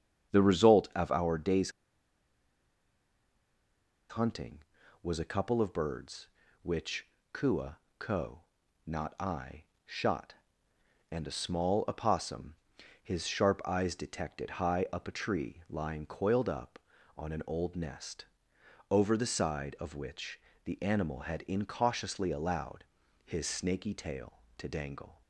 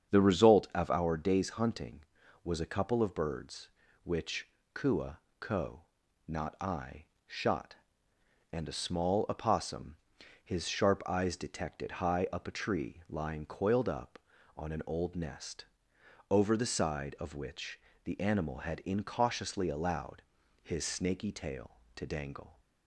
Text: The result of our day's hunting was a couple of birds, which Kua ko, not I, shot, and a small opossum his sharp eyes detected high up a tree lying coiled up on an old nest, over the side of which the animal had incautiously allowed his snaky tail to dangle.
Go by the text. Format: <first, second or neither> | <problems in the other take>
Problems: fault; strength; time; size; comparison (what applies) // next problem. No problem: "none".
second | starts louder than the rest; strong; until 1.3 s; 7.5 dB; strong in the second // pauses between "day's" and "hunting"; strong; at 1.7 s; 2.3 s long // pauses between "which" and "Kua"; slight; at 7.0 s; 0.24 s long; slight in the second // pauses between "Kua" and "ko"; slight; at 7.7 s; 0.20 s long; slight in the second // pauses between "opossum" and "his"; noticeable; at 12.5 s; 0.46 s long; noticeable in the second // pauses between "which" and "the"; slight; at 20.3 s; 0.28 s long; slight in the second // pauses between "allowed" and "his"; at 22.8 s; 0.40 s long; also in the second